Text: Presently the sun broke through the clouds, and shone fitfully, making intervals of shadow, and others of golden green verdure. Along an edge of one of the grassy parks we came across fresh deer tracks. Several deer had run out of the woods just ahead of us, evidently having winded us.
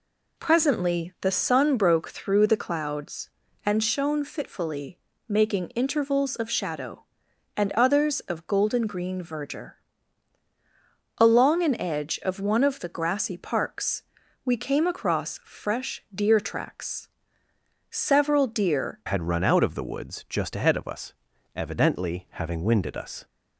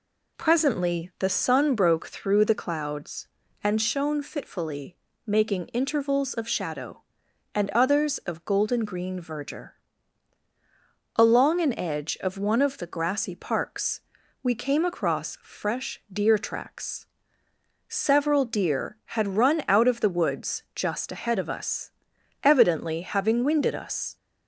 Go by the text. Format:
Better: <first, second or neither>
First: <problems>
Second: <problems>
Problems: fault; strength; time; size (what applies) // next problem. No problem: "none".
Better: second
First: pauses between "parks" and "we"; at 14.0 s; 0.42 s long // changes voice at "had"; from 19.0 s on; 4.2 s long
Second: pauses between "parks" and "we"; at 14.0 s; 0.42 s long